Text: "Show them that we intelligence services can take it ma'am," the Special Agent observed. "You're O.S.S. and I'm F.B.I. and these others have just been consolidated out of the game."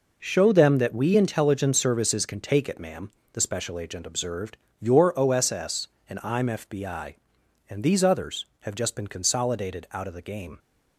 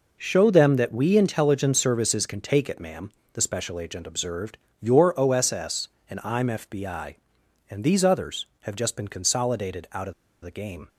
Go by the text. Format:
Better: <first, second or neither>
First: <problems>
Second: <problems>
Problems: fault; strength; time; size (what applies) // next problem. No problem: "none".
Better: first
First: none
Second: pauses between "of" and "the"; slight; at 10.1 s; 0.30 s long